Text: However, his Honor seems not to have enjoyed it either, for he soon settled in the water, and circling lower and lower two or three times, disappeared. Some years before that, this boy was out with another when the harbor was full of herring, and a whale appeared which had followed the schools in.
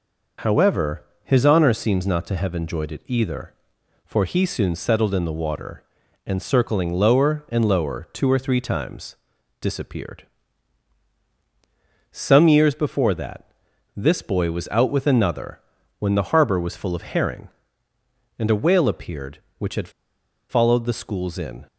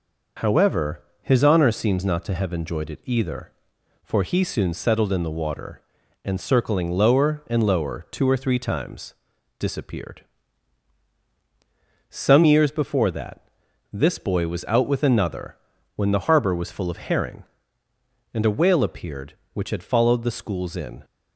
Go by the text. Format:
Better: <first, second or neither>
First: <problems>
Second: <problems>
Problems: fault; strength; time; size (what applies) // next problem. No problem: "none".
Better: second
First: pauses between "another" and "when"; at 15.5 s; 0.40 s long // pauses between "had" and "followed"; noticeable; at 19.8 s; 0.60 s long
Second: pauses between "another" and "when"; at 15.5 s; 0.40 s long